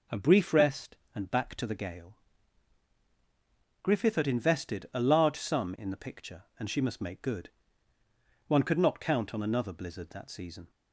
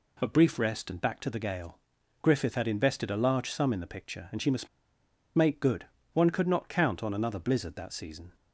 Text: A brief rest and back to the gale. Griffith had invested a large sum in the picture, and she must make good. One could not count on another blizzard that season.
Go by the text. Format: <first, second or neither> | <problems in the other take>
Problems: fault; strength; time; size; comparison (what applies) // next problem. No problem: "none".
first | pauses between "must" and "make"; noticeable; at 4.6 s; 0.67 s long